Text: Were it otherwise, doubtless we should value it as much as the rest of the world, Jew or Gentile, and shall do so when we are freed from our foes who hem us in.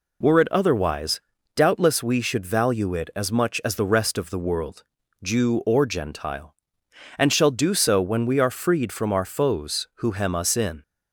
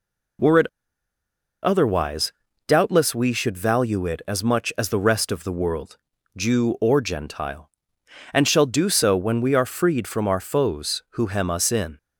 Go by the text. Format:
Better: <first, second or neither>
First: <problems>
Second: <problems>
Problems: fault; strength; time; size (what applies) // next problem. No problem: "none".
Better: first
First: none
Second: pauses between "it" and "otherwise"; noticeable; at 0.6 s; 0.97 s long